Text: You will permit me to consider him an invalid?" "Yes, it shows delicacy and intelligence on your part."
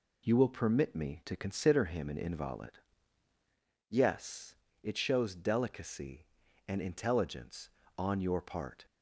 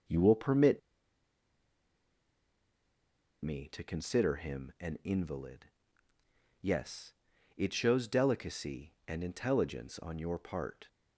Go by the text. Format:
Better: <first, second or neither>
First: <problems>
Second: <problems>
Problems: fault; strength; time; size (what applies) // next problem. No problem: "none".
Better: first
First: none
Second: pauses between "permit" and "me"; strong; at 0.7 s; 2.6 s long